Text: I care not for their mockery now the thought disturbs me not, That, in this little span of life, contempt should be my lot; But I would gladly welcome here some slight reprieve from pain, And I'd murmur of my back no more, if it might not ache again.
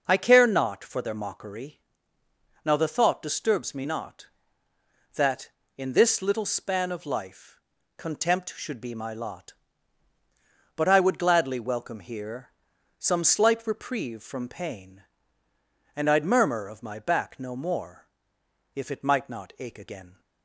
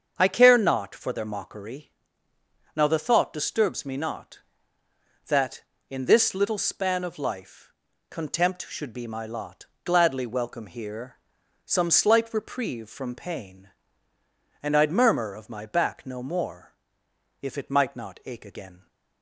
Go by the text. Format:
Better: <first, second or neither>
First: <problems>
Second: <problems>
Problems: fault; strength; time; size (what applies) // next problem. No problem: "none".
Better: first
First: pauses between "mockery" and "now"; noticeable; at 1.7 s; 0.86 s long // pauses between "here" and "some"; noticeable; at 12.5 s; 0.48 s long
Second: starts louder than the rest; until 1.1 s; 7 dB // pauses between "mockery" and "now"; noticeable; at 1.8 s; 0.86 s long // skips "But I would"; at 9.7 s // pauses between "here" and "some"; noticeable; at 11.1 s; 0.48 s long